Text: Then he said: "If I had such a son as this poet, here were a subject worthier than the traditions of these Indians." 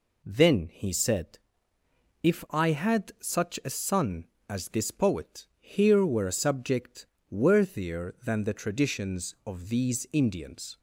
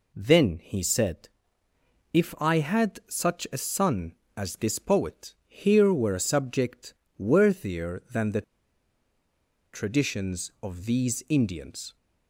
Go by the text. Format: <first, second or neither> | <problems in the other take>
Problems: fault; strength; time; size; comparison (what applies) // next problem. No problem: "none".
first | pauses between "subject" and "worthier"; slight; at 6.9 s; 0.24 s long; slight in the first // pauses between "the" and "traditions"; strong; at 8.4 s; 1.3 s long